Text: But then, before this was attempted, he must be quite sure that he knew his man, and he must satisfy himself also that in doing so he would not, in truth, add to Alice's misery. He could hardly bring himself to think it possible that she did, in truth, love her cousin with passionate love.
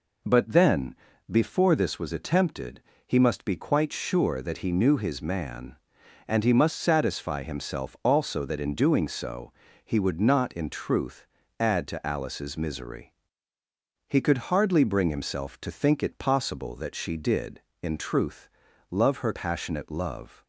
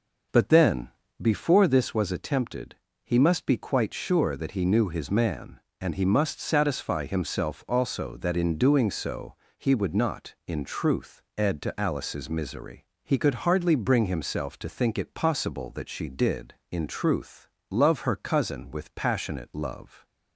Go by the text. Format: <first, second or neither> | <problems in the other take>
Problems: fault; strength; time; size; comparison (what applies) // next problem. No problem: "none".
second | pauses between "so" and "he"; slight; at 9.5 s; 0.32 s long; slight in the second // skips "cousin with"; at 19.3 s